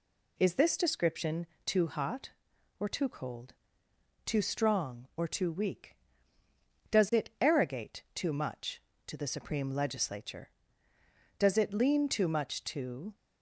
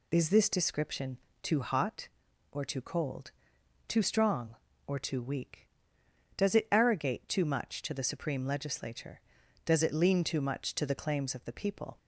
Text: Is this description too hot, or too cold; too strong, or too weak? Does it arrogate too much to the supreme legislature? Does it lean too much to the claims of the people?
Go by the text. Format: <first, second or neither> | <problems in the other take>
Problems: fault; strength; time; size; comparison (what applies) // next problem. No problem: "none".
second | pauses between "description" and "too"; slight; at 1.4 s; 0.18 s long; slight in the second // stops before "the claims of the people"; at 13.1 s